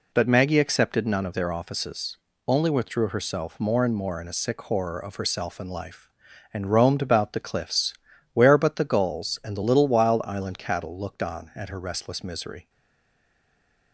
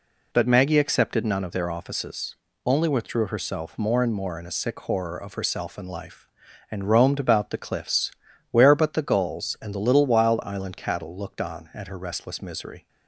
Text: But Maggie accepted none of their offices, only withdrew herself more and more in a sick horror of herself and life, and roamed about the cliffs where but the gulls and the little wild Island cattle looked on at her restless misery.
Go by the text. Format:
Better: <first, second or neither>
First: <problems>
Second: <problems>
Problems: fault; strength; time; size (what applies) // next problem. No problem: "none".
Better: second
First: pauses between "cliffs" and "where"; at 7.9 s; 0.40 s long // stays silent after the last word; noticeable; from 12.6 s on; 1.3 s long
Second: pauses between "cliffs" and "where"; at 8.1 s; 0.40 s long